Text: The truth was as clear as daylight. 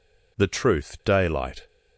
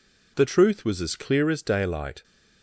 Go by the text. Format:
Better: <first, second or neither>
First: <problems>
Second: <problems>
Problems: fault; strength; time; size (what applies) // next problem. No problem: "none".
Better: second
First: skips "was as clear as"; at 1.0 s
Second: none